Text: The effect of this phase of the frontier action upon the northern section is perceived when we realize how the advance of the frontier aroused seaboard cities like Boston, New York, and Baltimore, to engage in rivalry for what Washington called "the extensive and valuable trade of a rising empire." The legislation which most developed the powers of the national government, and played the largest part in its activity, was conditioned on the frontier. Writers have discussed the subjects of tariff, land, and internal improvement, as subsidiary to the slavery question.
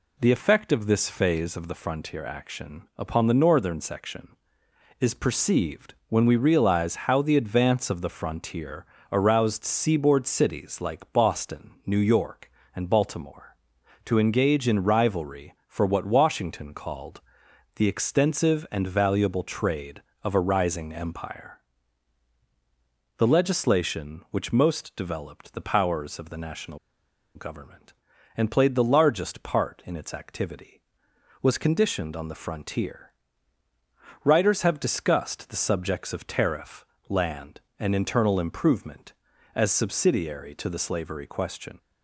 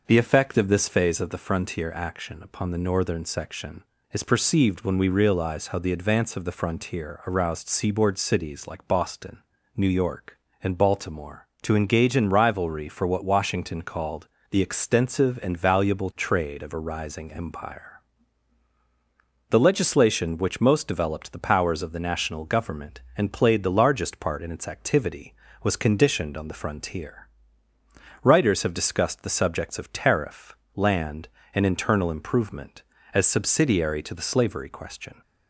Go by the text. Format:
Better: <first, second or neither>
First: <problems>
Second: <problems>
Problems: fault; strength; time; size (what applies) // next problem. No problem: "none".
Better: second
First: pauses between "perceived" and "when"; slight; at 5.9 s; 0.16 s long // pauses between "frontier" and "aroused"; slight; at 8.8 s; 0.26 s long // pauses between "called" and "the"; noticeable; at 17.2 s; 0.54 s long // pauses between "national" and "government"; noticeable; at 26.7 s; 0.57 s long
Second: pauses between "called" and "the"; slight; at 14.2 s; 0.24 s long